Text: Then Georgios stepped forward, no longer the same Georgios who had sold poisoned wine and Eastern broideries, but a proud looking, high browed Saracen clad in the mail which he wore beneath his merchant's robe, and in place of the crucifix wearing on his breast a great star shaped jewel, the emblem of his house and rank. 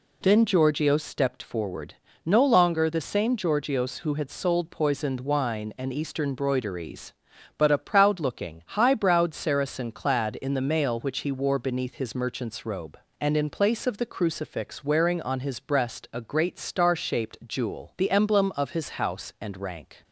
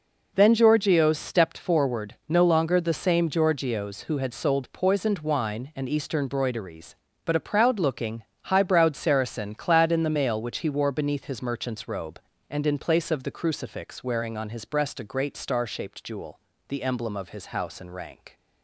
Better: neither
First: none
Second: none

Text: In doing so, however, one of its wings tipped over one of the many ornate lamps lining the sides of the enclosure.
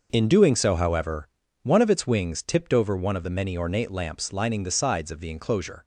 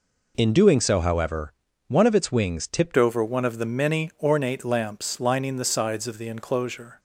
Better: first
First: none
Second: changes voice at "over"; from 2.9 s on; 4.0 s long

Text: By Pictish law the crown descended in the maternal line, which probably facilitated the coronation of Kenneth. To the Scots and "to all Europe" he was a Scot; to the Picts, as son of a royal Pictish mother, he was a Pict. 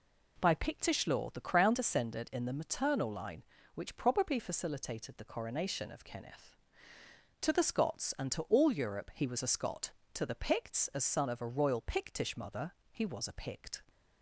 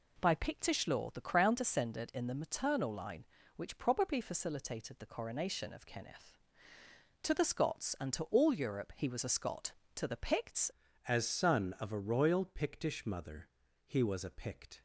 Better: first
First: none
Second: changes voice at "as"; from 11.0 s on; 3.8 s long

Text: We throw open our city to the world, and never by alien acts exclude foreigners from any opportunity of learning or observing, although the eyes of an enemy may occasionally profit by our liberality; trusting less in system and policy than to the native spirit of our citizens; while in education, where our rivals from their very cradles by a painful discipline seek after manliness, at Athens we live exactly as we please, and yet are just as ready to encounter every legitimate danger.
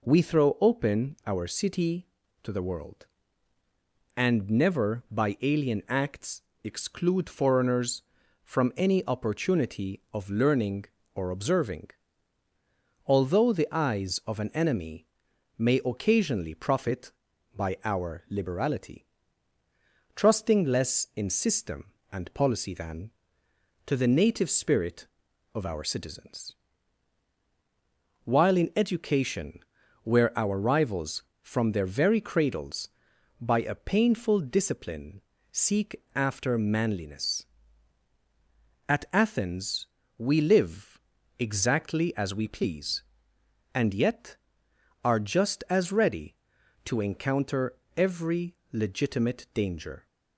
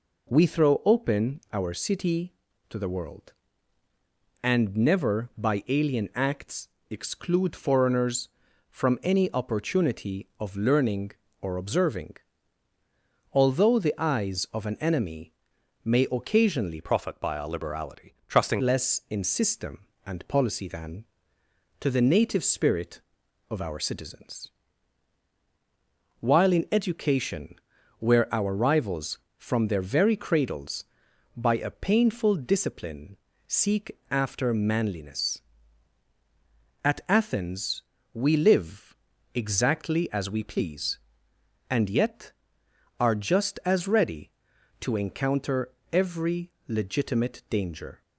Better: first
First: pauses between "acts" and "exclude"; slight; at 6.4 s; 0.22 s long // pauses between "enemy" and "may"; noticeable; at 15.0 s; 0.50 s long // pauses between "discipline" and "seek"; slight; at 35.1 s; 0.32 s long // pauses between "seek" and "after"; slight; at 35.9 s; 0.16 s long // pauses between "Athens" and "we"; slight; at 39.8 s; 0.30 s long // pauses between "live" and "exactly"; at 40.9 s; 0.40 s long // pauses between "encounter" and "every"; slight; at 47.7 s; 0.22 s long // pauses between "every" and "legitimate"; slight; at 48.5 s; 0.18 s long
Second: pauses between "acts" and "exclude"; slight; at 6.6 s; 0.22 s long // pauses between "enemy" and "may"; noticeable; at 15.3 s; 0.50 s long // changes voice from "profit" to "trusting"; from 16.8 to 18.6 s; 1.8 s long // pauses between "discipline" and "seek"; slight; at 33.1 s; 0.32 s long // pauses between "seek" and "after"; slight; at 33.9 s; 0.16 s long // pauses between "Athens" and "we"; slight; at 37.8 s; 0.30 s long // pauses between "live" and "exactly"; at 38.9 s; 0.40 s long // pauses between "encounter" and "every"; slight; at 45.6 s; 0.22 s long // pauses between "every" and "legitimate"; slight; at 46.4 s; 0.18 s long

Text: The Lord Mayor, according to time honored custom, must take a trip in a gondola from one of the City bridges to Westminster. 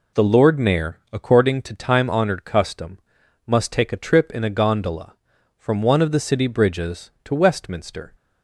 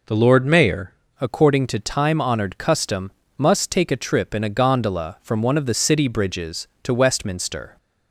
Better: first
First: none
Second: changes voice at "according"; from 1.2 s on; 6.5 s long

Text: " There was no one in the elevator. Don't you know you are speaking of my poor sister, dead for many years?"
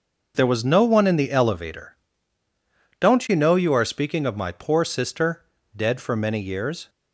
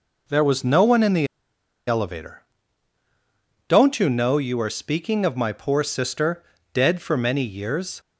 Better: first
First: none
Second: pauses between "the" and "elevator"; noticeable; at 1.2 s; 0.61 s long

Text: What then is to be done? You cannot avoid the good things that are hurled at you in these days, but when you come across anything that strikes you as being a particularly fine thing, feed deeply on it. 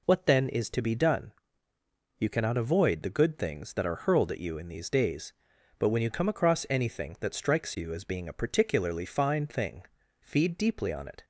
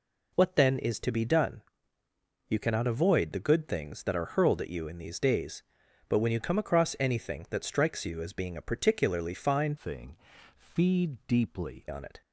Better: first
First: none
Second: changes voice from "thing" to "deeply"; from 9.7 to 11.8 s; 2.1 s long

